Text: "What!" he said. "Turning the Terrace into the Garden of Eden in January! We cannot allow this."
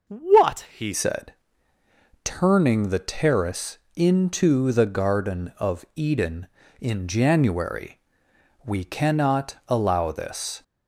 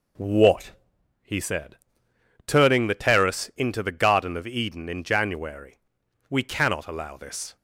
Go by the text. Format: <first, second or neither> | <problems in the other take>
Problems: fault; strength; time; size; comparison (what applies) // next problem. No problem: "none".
second | changes voice at "said"; from 0.9 s on; 9.7 s long // pauses between "Terrace" and "into"; slight; at 3.7 s; 0.18 s long